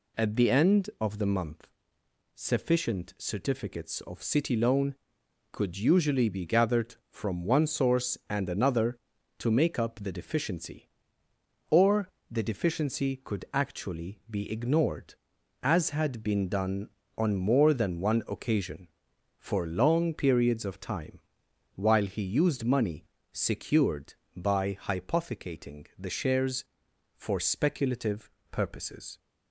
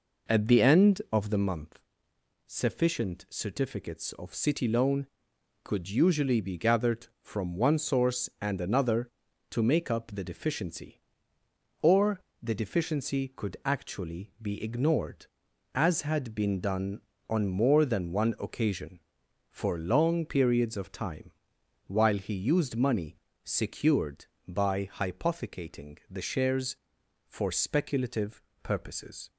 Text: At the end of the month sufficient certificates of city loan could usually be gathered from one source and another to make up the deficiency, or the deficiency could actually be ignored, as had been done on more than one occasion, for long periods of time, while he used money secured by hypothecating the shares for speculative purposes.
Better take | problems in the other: first | starts louder than the rest; noticeable; until 1.4 s; 4.5 dB // pauses between "month" and "sufficient"; noticeable; at 1.7 s; 0.66 s long; noticeable in the first // pauses between "or" and "the"; slight; at 12.1 s; 0.22 s long; slight in the first // pauses between "money" and "secured"; slight; at 23.1 s; 0.28 s long; slight in the first // pauses between "speculative" and "purposes"; slight; at 28.4 s; 0.20 s long; slight in the first

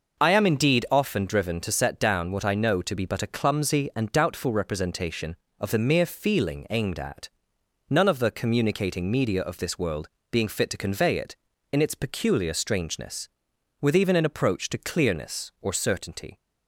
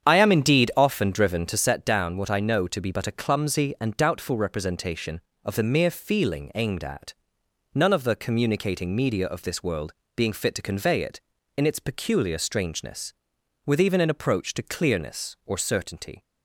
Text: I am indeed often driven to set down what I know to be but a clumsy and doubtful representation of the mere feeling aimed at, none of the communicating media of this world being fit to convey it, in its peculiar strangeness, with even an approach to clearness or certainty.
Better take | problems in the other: first | starts louder than the rest; strong; until 1.8 s; 8 dB // pauses between "world" and "being"; slight; at 9.9 s; 0.24 s long; slight in the first

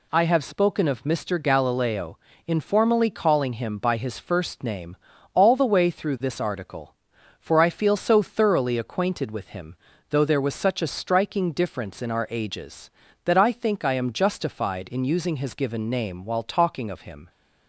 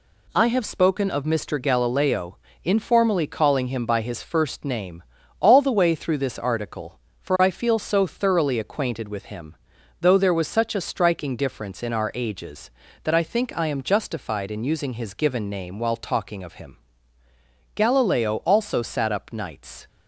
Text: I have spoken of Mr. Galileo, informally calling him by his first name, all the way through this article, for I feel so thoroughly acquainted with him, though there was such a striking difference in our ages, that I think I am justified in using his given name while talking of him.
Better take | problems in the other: first | goes on to say "Galileo also sat up nights"; strong; from 17.7 s on; 2.1 s long

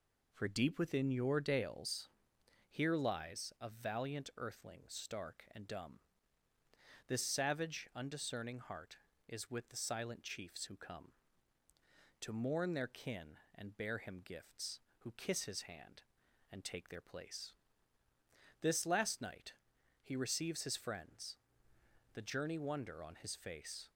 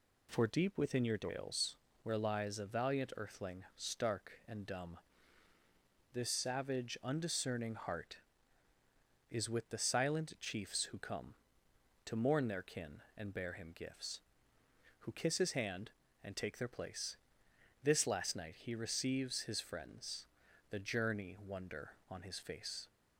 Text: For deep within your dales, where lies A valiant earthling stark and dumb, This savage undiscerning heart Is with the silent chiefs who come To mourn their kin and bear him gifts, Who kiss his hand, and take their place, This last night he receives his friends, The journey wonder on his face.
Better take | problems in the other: second | says "here" for "where"; at 2.6 s // pauses between "night" and "he"; noticeable; at 19.5 s; 0.48 s long

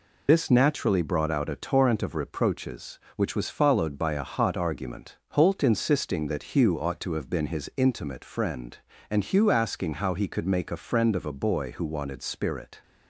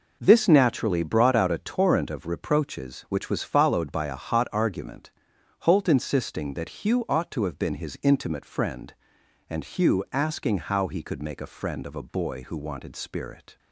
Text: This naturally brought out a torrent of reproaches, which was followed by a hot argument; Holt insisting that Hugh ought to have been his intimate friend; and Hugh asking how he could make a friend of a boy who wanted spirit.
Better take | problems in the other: second | loses the start of "This"; at 0.2 s; 60 ms

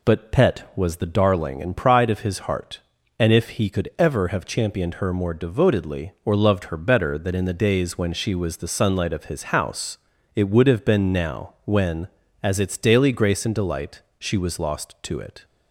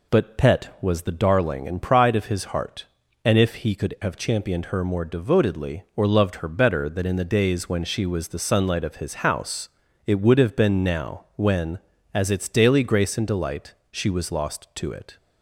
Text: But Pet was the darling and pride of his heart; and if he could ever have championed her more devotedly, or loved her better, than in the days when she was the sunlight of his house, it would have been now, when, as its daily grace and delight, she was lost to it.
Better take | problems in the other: first | skips "ever"; at 3.9 s

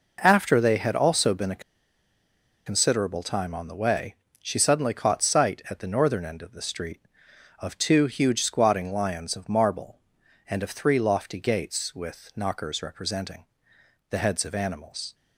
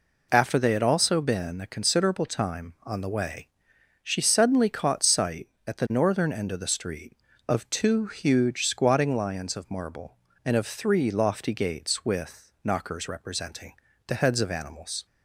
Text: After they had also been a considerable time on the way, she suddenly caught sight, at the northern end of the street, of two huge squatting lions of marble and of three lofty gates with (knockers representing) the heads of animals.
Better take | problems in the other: second | pauses between "a" and "considerable"; at 1.6 s; 1.0 s long

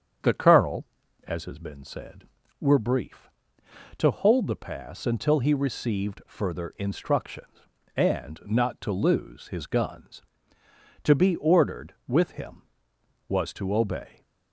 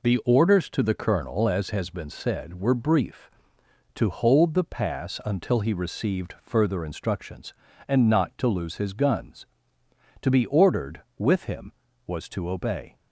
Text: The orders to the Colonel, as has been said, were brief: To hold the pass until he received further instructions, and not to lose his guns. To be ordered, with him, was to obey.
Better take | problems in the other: second | starts louder than the rest; strong; until 1.6 s; 8 dB // skips "orders to the"; at 0.3 s

